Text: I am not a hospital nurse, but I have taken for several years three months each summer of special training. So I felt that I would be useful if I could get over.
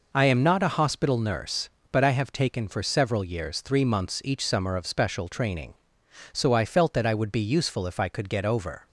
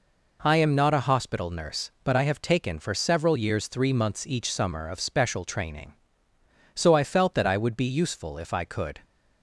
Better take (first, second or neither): first